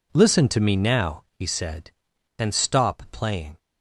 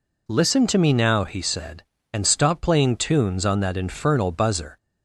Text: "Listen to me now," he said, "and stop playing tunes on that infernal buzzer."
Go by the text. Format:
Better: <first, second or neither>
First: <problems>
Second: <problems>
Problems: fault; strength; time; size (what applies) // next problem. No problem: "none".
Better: second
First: stops before "tunes on that infernal buzzer"; at 3.5 s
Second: none